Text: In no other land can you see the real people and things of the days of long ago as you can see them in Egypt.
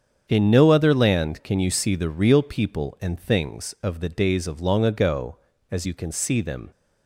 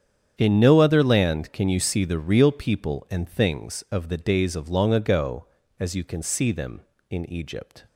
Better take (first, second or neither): second